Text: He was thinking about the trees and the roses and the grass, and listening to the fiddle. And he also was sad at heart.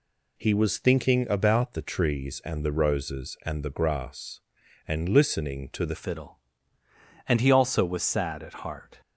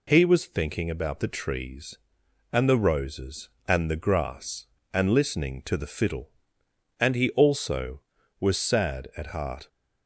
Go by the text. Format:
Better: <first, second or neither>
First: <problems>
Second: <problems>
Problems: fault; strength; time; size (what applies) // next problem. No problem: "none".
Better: second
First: changes voice at "fiddle"; from 5.9 s on; 3.0 s long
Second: none